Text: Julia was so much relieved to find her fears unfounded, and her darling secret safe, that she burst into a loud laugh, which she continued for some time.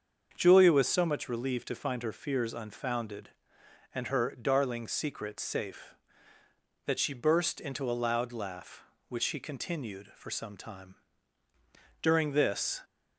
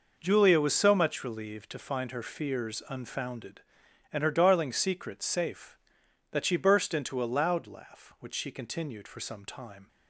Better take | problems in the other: second | starts louder than the rest; until 1.3 s; 6.5 dB // goes on to say "During this"; noticeable; from 12.0 s on; 0.80 s long

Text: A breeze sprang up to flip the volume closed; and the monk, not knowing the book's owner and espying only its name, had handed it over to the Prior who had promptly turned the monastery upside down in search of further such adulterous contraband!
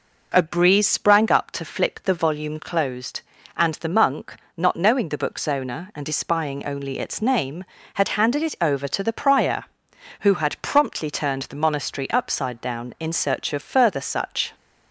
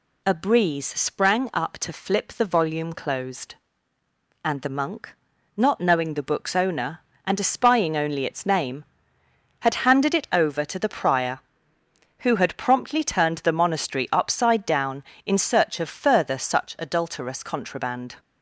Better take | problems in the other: second | stops before "adulterous contraband"; at 14.5 s

